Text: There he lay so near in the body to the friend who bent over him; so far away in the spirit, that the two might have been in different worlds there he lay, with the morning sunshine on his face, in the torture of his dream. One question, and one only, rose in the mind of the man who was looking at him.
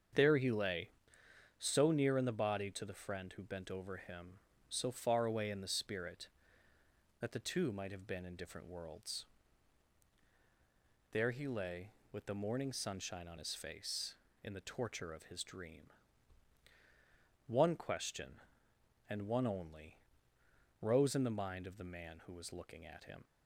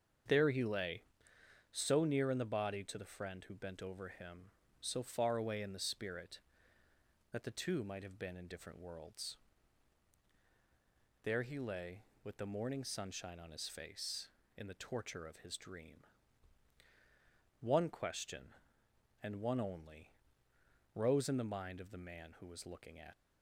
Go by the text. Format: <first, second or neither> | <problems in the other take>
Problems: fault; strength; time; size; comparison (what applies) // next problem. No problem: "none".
first | starts louder than the rest; strong; until 1.9 s; 7.5 dB; strong in the first // pauses between "worlds" and "there"; strong; at 9.3 s; 1.8 s long; strong in the first // stops before "him"; at 23.1 s